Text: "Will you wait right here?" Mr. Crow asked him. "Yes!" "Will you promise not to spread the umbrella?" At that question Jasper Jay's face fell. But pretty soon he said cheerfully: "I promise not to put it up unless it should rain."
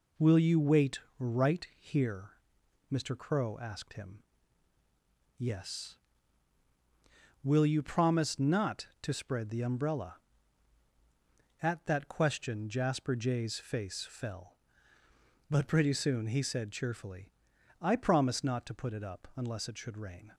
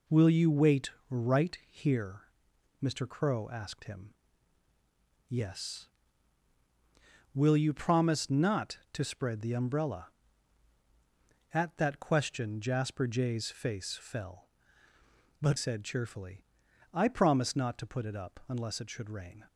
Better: first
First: pauses between "wait" and "right"; slight; at 0.9 s; 0.18 s long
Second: pauses between "wait" and "right"; slight; at 0.9 s; 0.18 s long // skips "pretty soon he"; at 15.5 s

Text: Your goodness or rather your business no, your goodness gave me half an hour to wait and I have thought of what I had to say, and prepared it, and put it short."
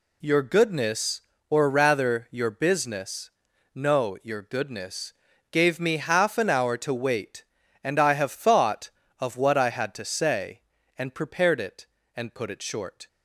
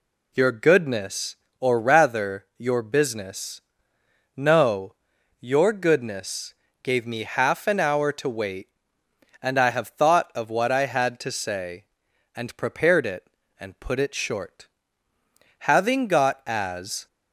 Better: first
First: pauses between "business" and "no"; at 3.3 s; 0.42 s long // pauses between "goodness" and "gave"; slight; at 5.1 s; 0.36 s long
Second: pauses between "business" and "no"; noticeable; at 3.6 s; 0.74 s long // pauses between "goodness" and "gave"; slight; at 6.5 s; 0.28 s long // goes on to say "Having got as"; from 15.5 s on; 1.4 s long

